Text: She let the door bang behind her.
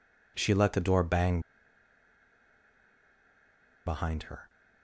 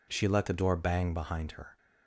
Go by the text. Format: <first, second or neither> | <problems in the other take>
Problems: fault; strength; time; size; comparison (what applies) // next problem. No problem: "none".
second | pauses between "bang" and "behind"; strong; at 1.3 s; 2.4 s long